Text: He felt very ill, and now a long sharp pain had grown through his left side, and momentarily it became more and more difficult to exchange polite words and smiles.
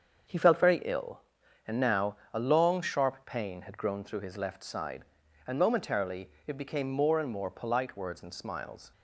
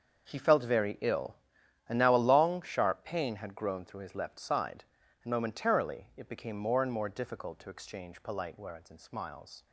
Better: second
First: starts louder than the rest; until 1.7 s; 7 dB // pauses between "now" and "a"; slight; at 2.1 s; 0.16 s long // pauses between "momentarily" and "it"; slight; at 6.2 s; 0.16 s long // skips "difficult to exchange"; at 7.4 s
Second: starts louder than the rest; until 1.3 s; 6.5 dB

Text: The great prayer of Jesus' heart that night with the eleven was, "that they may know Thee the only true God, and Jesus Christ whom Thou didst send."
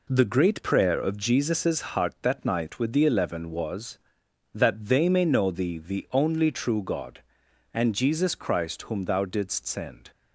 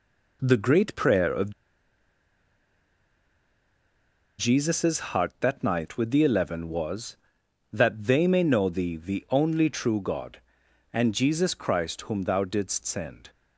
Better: first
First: none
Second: pauses between "of" and "Jesus"; strong; at 1.5 s; 2.8 s long

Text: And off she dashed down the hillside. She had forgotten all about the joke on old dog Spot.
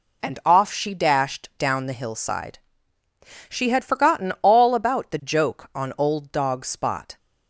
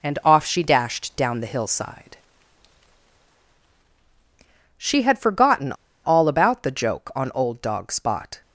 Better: first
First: none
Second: pauses between "forgotten" and "all"; slight; at 5.7 s; 0.31 s long

